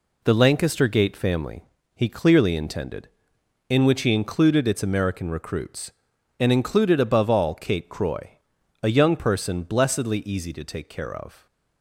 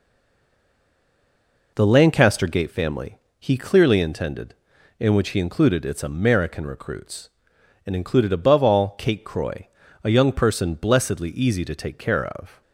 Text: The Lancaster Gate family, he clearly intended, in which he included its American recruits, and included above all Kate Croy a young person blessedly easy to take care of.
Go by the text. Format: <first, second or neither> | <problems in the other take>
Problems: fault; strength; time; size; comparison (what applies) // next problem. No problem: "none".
first | stays silent before the first word; noticeable; until 1.7 s; 1.7 s long // pauses between "Croy" and "a"; slight; at 9.6 s; 0.36 s long; noticeable in the first